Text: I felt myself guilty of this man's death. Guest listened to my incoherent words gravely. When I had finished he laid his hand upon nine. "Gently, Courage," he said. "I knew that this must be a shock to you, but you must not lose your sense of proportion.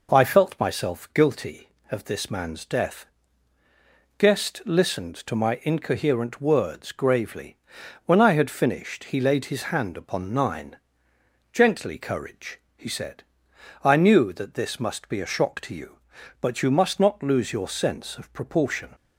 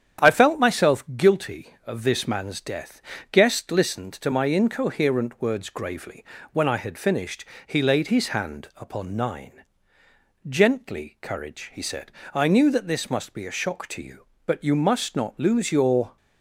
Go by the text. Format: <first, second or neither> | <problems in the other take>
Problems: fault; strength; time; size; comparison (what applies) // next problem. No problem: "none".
first | starts louder than the rest; strong; until 1.3 s; 9.5 dB // pauses between "finished" and "he"; slight; at 7.4 s; 0.24 s long // stops before "sense of proportion"; at 16.1 s